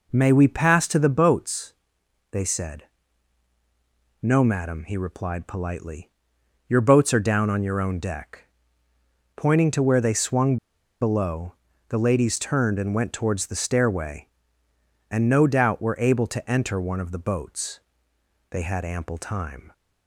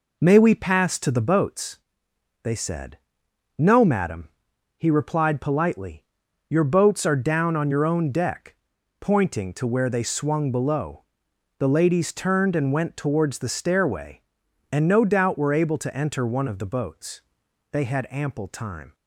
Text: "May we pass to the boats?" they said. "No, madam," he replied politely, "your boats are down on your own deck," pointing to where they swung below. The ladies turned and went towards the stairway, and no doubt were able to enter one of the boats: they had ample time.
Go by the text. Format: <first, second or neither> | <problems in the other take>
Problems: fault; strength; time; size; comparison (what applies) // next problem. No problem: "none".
second | pauses between "swung" and "below"; at 10.5 s; 0.45 s long